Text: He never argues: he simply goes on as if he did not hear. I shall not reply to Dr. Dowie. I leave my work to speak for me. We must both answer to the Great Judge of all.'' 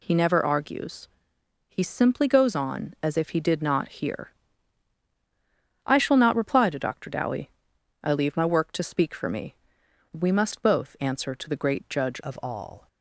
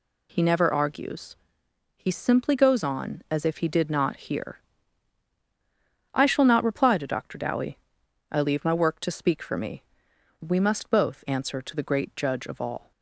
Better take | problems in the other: second | changes voice at "of"; from 12.2 s on; 0.6 s long

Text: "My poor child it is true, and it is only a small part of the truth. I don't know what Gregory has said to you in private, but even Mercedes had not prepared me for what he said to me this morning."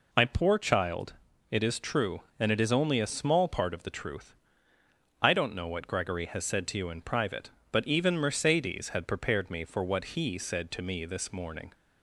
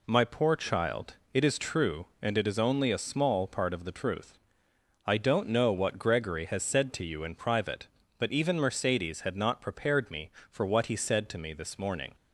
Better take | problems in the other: second | pauses between "child" and "it"; at 1.1 s; 0.38 s long; slight in the second // skips "not"; at 9.0 s

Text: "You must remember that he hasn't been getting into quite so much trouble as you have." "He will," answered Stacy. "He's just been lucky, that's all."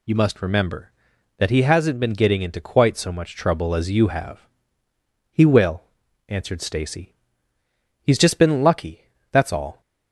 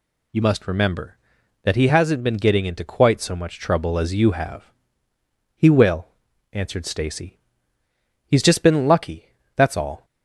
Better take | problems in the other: neither | none

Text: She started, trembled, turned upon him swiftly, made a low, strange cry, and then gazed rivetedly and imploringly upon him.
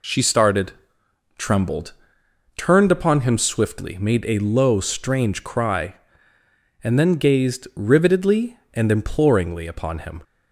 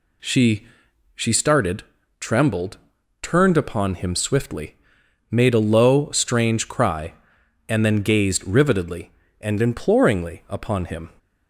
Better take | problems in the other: first | says "She" twice; at 1.1 s

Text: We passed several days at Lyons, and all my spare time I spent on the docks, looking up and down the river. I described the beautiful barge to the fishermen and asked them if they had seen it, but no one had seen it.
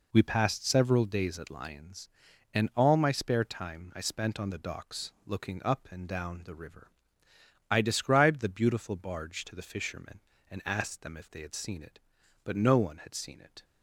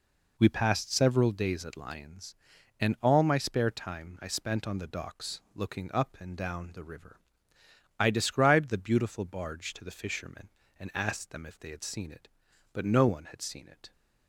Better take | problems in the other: neither | none

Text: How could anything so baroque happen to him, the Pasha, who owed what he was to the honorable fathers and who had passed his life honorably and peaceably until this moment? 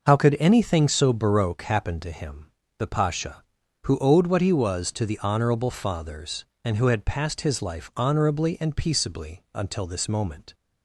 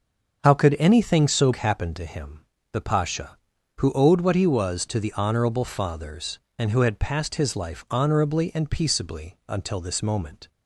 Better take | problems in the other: first | starts louder than the rest; until 1.4 s; 6.5 dB // skips "baroque"; at 1.5 s

